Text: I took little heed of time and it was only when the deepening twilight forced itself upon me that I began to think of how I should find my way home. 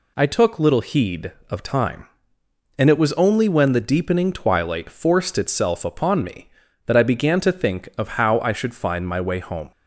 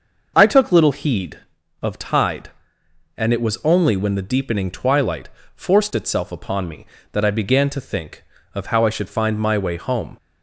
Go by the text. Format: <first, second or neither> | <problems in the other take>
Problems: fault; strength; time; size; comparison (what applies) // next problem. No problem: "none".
first | starts louder than the rest; noticeable; until 1.3 s; 6 dB // says "tide" for "time"; at 1.9 s // pauses between "twilight" and "forced"; slight; at 5.2 s; 0.24 s long